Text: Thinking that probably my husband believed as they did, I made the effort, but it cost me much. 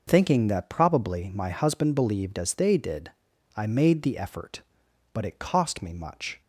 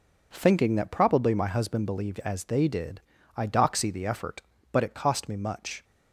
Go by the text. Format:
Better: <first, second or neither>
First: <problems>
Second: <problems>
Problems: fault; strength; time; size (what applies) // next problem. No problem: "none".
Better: first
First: none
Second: says "doxy" for "made"; at 3.4 s